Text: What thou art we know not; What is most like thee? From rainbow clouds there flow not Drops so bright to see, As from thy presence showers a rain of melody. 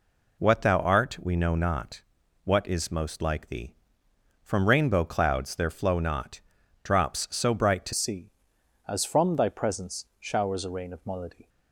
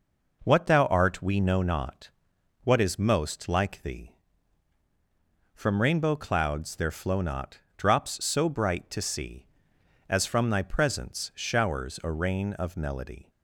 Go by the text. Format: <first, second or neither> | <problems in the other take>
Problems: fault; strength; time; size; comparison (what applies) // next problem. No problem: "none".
second | pauses between "not" and "Drops"; at 6.3 s; 0.42 s long; slight in the second // changes voice at "see"; from 7.9 s on; 3.5 s long